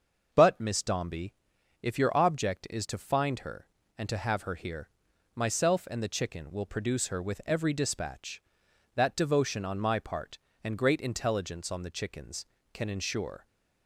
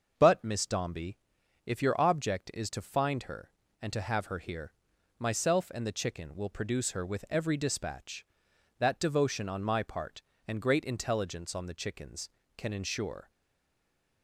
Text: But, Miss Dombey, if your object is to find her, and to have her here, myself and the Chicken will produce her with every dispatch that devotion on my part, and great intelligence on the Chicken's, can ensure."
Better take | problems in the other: first | starts louder than the rest; until 1.1 s; 6 dB; also in the first // stays silent after the last word; from 13.2 s on; 1.0 s long

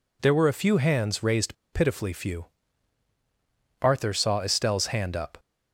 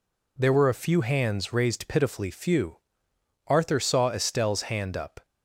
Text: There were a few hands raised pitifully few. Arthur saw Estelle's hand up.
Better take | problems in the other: second | pauses between "raised" and "pitifully"; slight; at 1.5 s; 0.18 s long

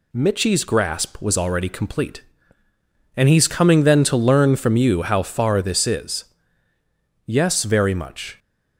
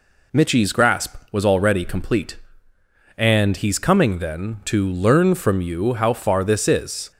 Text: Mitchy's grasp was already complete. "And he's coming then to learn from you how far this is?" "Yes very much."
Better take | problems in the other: first | stops before "Yes very much"; at 7.1 s

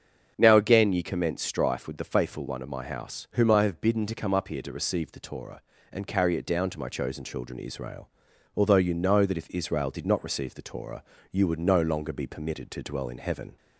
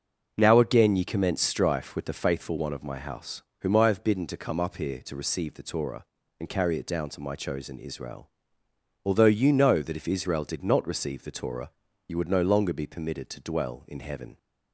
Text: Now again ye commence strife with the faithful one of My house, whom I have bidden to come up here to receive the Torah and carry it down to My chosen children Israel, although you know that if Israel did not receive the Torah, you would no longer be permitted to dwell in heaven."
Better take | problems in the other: first | starts louder than the rest; noticeable; until 1.3 s; 6 dB; strong in the first // skips "children"; at 7.7 s

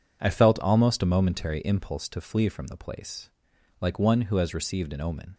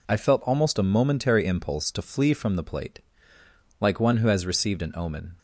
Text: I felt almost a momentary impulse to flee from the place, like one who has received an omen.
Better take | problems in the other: first | says "plate" for "place"; at 2.6 s

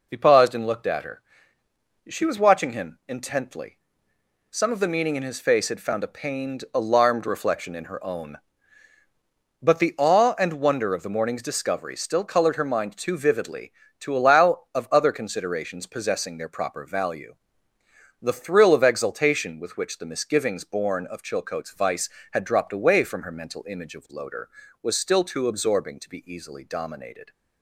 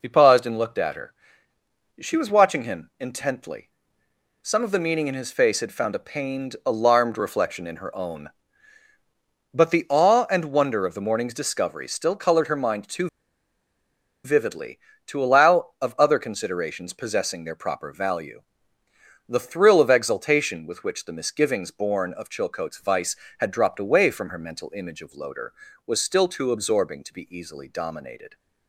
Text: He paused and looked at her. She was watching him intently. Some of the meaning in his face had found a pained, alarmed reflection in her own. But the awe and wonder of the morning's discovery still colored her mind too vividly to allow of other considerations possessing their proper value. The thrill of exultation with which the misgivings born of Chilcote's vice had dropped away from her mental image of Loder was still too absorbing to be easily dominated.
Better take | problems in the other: first | pauses between "too" and "vividly"; at 13.0 s; 1.1 s long

